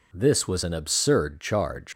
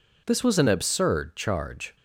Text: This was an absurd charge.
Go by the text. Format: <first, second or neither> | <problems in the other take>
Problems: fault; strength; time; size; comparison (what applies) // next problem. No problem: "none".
second | leaves "charge" unfinished; at 1.9 s; 80 ms